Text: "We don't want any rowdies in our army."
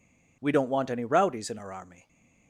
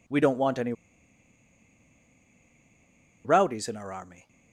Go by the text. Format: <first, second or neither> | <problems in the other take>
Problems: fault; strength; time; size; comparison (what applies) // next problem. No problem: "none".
first | pauses between "any" and "rowdies"; strong; at 0.7 s; 2.5 s long